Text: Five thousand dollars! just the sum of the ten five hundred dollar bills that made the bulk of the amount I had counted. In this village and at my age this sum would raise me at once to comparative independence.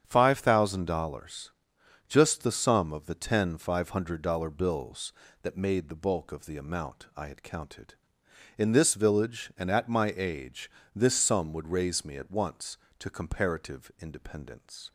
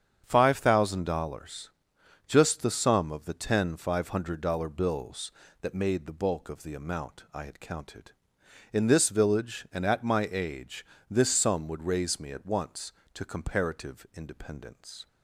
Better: neither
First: starts louder than the rest; strong; until 1.0 s; 8 dB // pauses between "age" and "this"; slight; at 10.6 s; 0.26 s long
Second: starts louder than the rest; strong; until 1.2 s; 8 dB // pauses between "age" and "this"; slight; at 10.8 s; 0.26 s long

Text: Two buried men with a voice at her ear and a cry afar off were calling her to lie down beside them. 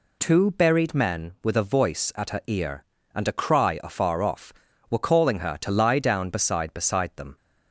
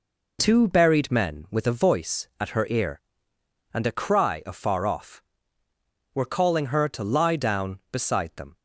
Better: second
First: says "beside" twice; at 6.7 s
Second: none

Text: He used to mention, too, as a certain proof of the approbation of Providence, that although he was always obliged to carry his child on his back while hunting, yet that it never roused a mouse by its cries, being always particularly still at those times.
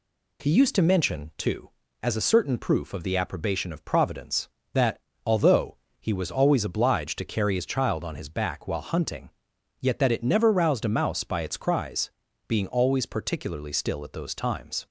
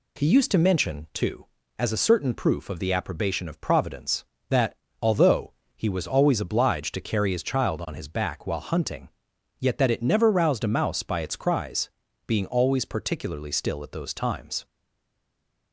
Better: first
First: pauses between "that" and "although"; slight; at 4.9 s; 0.24 s long // pauses between "although" and "he"; slight; at 5.7 s; 0.22 s long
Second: pauses between "that" and "although"; slight; at 4.7 s; 0.24 s long // pauses between "although" and "he"; slight; at 5.5 s; 0.22 s long // stays silent after the last word; from 14.6 s on; 1.1 s long

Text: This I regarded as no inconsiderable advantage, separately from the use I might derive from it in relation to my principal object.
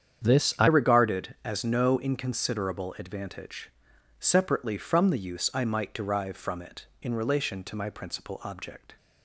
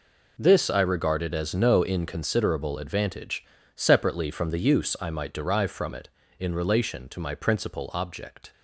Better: second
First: starts louder than the rest; strong; until 1.2 s; 8.5 dB // changes voice at "regarded"; from 0.6 s on; 8.3 s long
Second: none

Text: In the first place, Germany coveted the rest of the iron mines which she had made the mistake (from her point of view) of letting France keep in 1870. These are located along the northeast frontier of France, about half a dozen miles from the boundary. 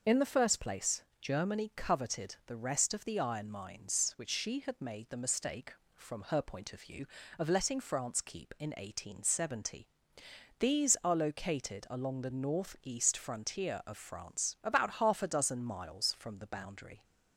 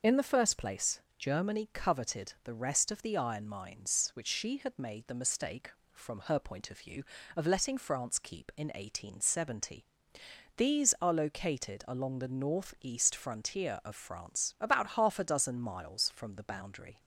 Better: neither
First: none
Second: none

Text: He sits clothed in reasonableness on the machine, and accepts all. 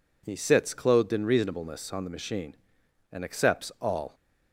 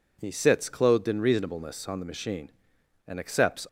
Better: first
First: none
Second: stops before "all"; at 3.6 s

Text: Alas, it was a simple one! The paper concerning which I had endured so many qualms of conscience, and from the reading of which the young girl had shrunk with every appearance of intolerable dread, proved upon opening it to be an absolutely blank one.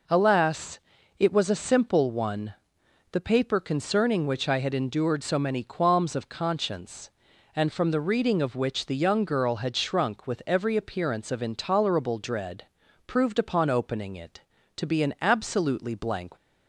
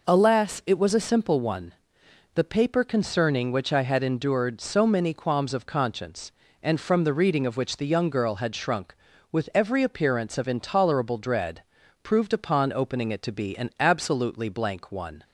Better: second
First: stops before "one"; at 16.3 s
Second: none

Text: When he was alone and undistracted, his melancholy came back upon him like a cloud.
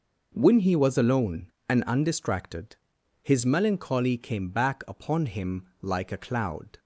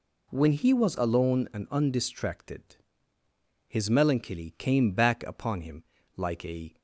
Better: first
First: none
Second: pauses between "him" and "like"; slight; at 5.8 s; 0.34 s long // stops before "cloud"; at 6.7 s

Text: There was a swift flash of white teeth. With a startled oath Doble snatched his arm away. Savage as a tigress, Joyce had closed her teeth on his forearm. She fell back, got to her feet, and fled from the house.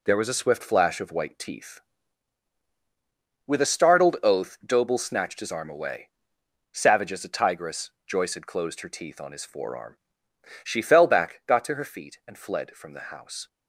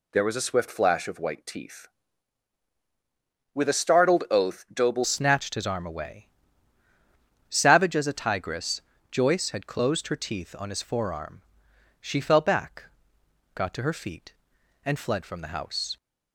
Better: first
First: none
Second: changes voice at "snatched"; from 5.0 s on; 10.9 s long

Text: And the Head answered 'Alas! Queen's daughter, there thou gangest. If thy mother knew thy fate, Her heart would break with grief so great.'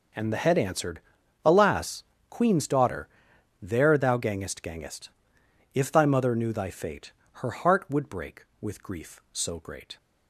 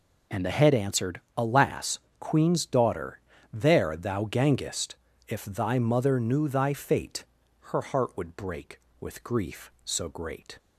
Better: second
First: pauses between "answered" and "Alas"; at 1.0 s; 0.44 s long // says "gangest" twice; at 4.6 s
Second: pauses between "answered" and "Alas"; slight; at 1.1 s; 0.16 s long

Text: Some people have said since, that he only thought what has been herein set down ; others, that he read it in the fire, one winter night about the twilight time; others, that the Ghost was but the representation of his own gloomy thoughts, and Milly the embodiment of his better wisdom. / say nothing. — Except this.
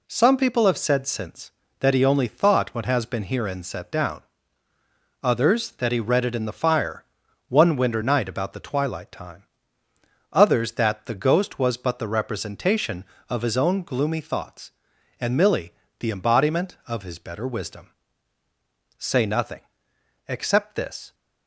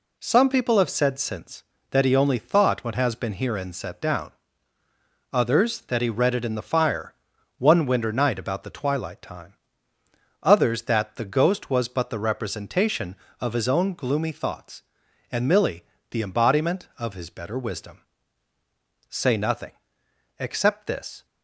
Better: neither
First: pauses between "Milly" and "the"; slight; at 15.7 s; 0.28 s long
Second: pauses between "Milly" and "the"; slight; at 15.8 s; 0.28 s long

